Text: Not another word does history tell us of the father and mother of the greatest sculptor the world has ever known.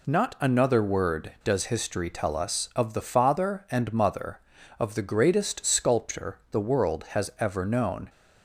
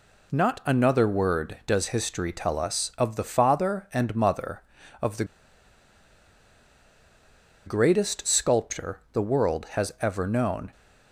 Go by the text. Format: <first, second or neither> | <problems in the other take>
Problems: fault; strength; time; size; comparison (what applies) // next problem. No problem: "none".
first | pauses between "the" and "greatest"; strong; at 5.2 s; 2.4 s long